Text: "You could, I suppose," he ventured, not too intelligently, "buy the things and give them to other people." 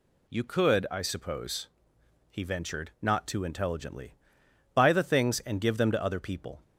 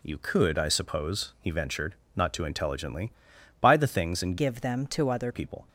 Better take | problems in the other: first | changes voice from "give" to "other"; from 4.3 to 5.3 s; 1.0 s long

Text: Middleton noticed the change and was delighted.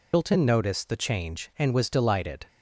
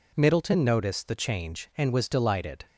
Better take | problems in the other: second | loses the start of "Middleton"; at 0.1 s; 195 ms

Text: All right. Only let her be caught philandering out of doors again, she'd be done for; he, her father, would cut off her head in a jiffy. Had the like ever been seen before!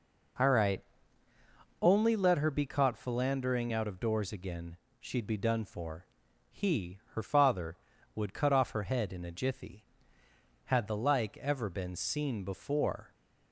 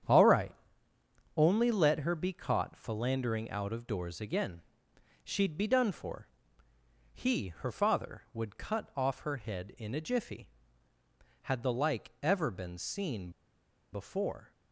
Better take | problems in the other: first | starts louder than the rest; strong; until 1.9 s; 9 dB // pauses between "seen" and "before"; noticeable; at 13.2 s; 0.63 s long

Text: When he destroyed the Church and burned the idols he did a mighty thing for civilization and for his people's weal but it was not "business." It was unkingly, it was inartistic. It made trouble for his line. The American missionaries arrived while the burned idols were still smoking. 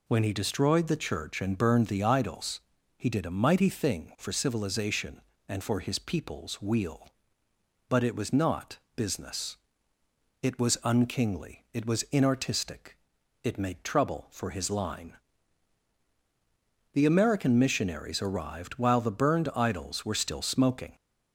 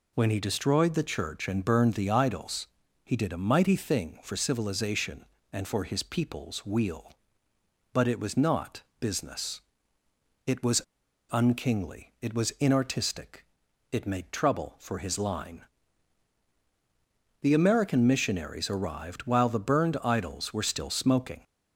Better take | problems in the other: first | pauses between "idols" and "he"; at 2.6 s; 0.38 s long; also in the first // pauses between "not" and "business"; slight; at 8.8 s; 0.18 s long; slight in the first // pauses between "was" and "unkingly"; noticeable; at 10.8 s; 0.48 s long

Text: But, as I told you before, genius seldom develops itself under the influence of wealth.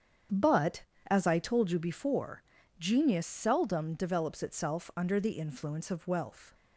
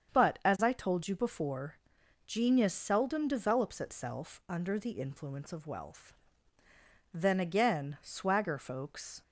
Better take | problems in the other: first | starts louder than the rest; strong; until 1.2 s; 7.5 dB; strong in the first // goes on to say "Then again swagger folks"; strong; from 7.1 s on; 2.0 s long

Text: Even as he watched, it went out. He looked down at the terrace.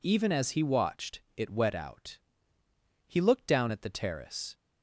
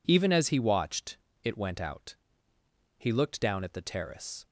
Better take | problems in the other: second | says "wet" for "went"; at 1.4 s

